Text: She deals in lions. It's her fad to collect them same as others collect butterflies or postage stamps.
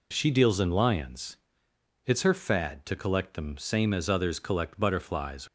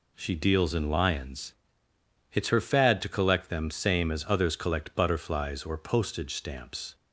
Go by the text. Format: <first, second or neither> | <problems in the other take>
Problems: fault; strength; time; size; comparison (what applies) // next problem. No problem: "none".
second | stops before "or postage stamps"; at 5.4 s